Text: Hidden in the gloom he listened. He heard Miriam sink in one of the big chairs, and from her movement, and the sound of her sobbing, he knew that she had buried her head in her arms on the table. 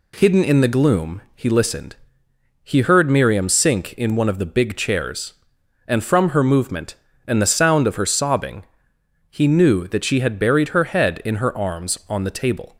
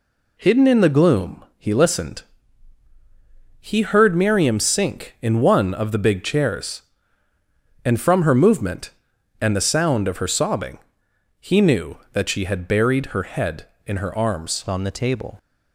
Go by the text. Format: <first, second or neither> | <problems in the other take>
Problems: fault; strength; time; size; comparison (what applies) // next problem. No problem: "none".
first | changes voice at "on"; from 14.6 s on; 0.7 s long